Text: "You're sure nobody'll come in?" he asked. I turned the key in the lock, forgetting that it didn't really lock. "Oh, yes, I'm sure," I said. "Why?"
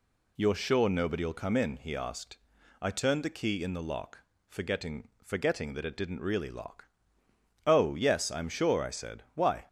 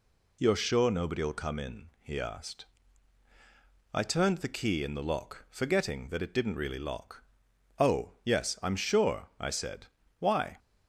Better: second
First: says "forgetting" twice; at 5.2 s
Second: none

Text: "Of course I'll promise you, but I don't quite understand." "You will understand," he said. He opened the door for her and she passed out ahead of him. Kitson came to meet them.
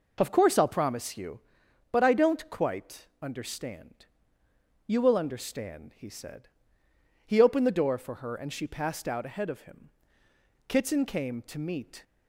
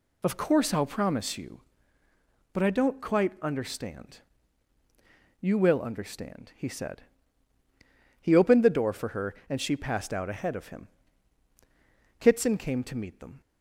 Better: second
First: stops before "them"; at 12.0 s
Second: none

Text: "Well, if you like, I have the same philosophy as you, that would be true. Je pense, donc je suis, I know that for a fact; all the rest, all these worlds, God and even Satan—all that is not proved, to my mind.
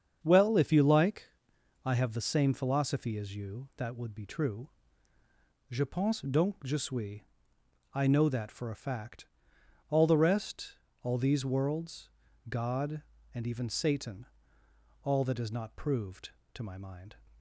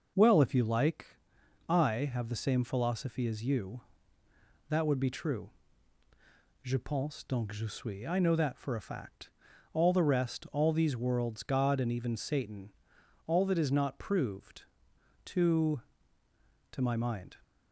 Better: first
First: starts louder than the rest; strong; until 1.2 s; 7.5 dB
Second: starts louder than the rest; noticeable; until 1.7 s; 6 dB // says "to" twice; at 16.6 s

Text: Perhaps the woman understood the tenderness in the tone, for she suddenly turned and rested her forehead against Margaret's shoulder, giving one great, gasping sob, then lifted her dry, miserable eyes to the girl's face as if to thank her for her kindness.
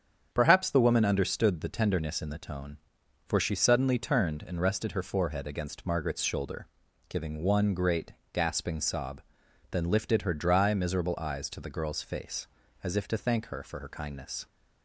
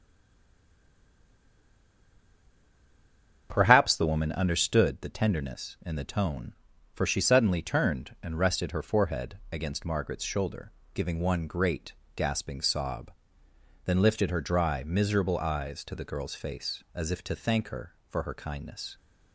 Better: first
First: starts louder than the rest; strong; until 1.3 s; 8 dB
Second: stays silent before the first word; strong; until 3.4 s; 3.4 s long // starts louder than the rest; strong; until 4.5 s; 7.5 dB

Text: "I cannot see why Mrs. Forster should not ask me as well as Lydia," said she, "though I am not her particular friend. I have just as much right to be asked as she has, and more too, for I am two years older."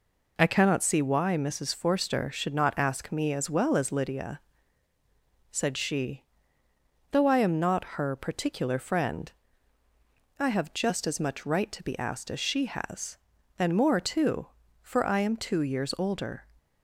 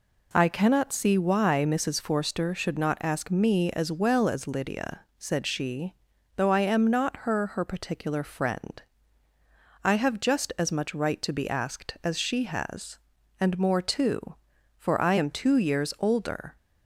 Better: first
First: none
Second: says "her" twice; at 7.4 s

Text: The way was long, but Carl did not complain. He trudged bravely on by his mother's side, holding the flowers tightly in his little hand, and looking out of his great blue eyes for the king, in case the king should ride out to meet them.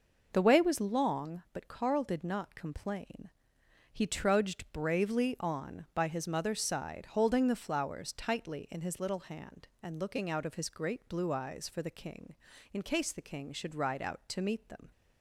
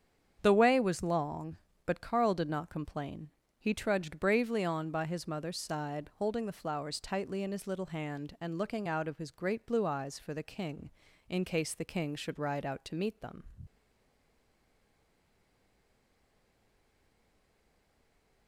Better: first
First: none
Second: starts louder than the rest; strong; until 1.4 s; 8 dB // stays silent after the last word; strong; from 13.6 s on; 4.8 s long

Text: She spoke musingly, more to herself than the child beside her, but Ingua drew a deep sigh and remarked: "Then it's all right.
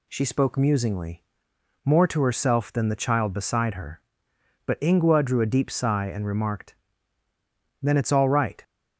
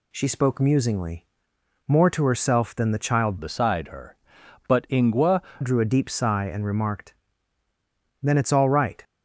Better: first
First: none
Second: changes voice from "beside" to "Ingua"; from 3.3 to 5.4 s; 2.1 s long

